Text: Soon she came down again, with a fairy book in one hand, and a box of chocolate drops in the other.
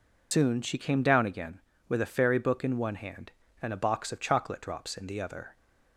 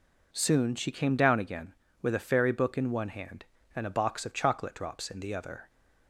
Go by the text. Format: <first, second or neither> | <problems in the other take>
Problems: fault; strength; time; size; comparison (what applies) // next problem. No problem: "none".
second | loses the start of "Soon"; at 0.3 s; 115 ms